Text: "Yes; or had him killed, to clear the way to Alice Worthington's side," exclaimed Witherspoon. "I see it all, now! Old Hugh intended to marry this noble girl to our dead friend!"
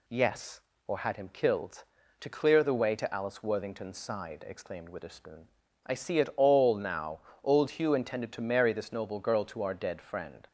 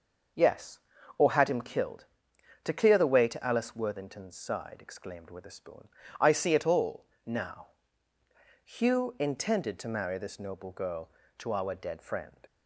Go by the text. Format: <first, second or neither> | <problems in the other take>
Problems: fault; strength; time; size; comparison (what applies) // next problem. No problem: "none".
first | skips "Old"; at 8.1 s